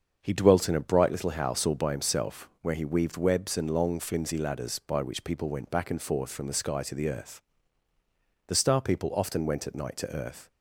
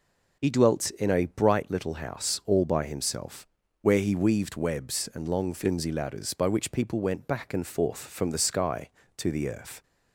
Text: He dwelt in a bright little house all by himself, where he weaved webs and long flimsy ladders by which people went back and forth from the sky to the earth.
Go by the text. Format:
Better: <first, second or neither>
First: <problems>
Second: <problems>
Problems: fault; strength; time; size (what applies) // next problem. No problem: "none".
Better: second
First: starts louder than the rest; until 1.2 s; 7 dB // goes on to say "The Star people often went at night to earth"; strong; from 8.4 s on; 2.0 s long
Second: none